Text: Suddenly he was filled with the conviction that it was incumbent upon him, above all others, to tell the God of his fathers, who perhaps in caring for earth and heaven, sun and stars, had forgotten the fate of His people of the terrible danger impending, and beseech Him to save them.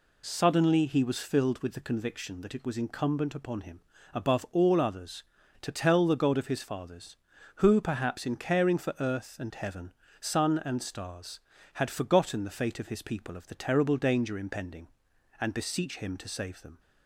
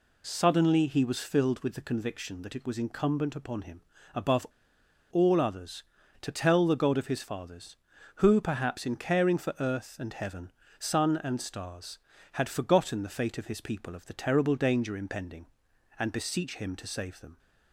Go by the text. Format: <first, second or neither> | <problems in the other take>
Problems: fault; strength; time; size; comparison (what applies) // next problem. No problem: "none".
first | pauses between "above" and "all"; noticeable; at 4.4 s; 0.65 s long